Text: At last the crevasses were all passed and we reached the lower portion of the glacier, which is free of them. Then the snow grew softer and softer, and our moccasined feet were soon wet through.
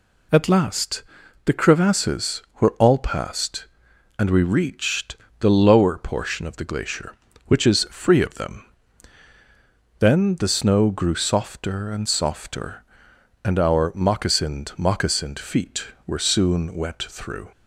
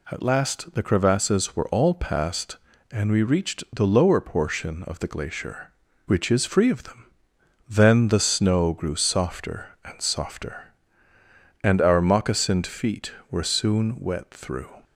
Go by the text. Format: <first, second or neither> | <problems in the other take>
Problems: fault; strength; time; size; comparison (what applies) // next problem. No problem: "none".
second | pauses between "last" and "the"; at 1.0 s; 0.42 s long // pauses between "reached" and "the"; slight; at 5.1 s; 0.24 s long // says "moccasined" twice; at 14.7 s